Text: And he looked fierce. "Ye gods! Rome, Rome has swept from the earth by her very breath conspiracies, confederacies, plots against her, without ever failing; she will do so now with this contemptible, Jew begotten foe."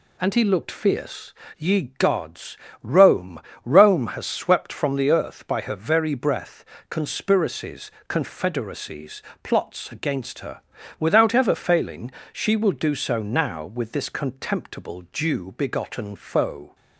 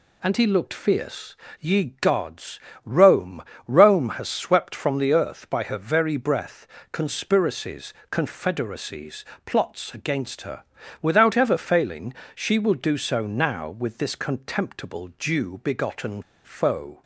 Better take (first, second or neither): first